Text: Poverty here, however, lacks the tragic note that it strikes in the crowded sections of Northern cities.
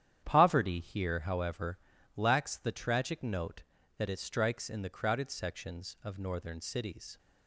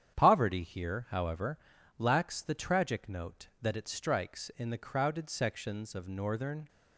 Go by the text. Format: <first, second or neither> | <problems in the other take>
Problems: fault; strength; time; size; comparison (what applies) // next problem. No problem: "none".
first | starts louder than the rest; strong; until 1.1 s; 9 dB; strong in the first // stops before "cities"; at 6.6 s